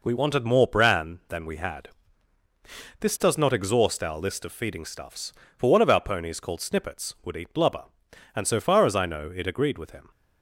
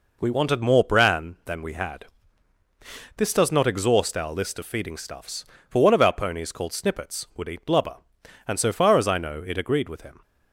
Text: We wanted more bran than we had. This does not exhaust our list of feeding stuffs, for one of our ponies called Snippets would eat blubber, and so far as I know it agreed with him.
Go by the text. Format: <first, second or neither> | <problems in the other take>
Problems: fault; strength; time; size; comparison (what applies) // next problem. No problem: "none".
neither | none